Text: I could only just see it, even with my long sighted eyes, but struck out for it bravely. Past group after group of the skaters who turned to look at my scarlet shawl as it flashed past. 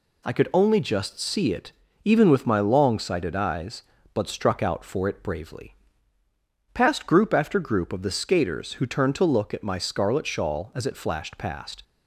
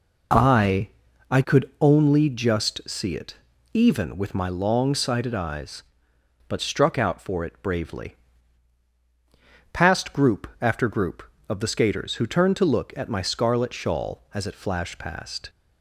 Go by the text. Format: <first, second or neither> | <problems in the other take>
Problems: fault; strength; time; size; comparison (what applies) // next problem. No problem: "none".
first | says "I" twice; at 1.2 s